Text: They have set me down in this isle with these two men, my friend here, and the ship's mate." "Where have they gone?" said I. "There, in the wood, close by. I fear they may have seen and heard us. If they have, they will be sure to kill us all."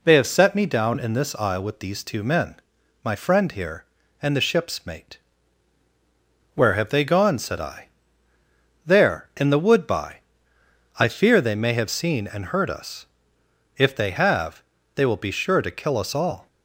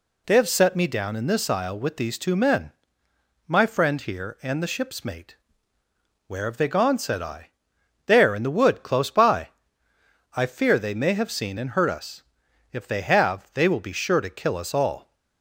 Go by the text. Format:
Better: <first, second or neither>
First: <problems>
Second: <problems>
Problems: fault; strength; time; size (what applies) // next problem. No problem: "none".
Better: second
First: skips "close"; at 9.8 s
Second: none